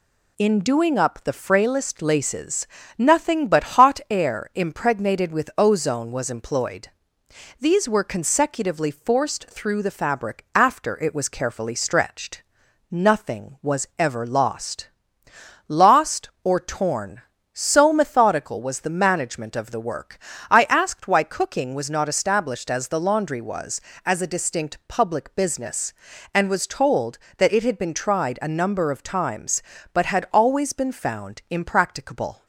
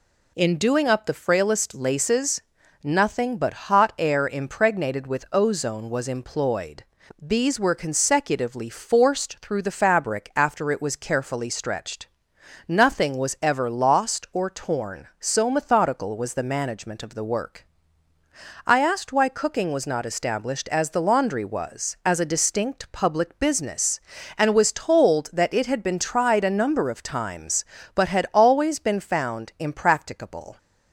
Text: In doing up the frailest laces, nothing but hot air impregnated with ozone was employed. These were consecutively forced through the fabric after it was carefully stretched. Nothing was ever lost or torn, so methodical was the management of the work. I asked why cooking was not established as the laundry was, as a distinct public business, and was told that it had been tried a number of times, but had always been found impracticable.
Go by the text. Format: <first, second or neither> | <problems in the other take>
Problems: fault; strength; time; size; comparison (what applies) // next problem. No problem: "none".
second | says "lost" twice; at 15.6 s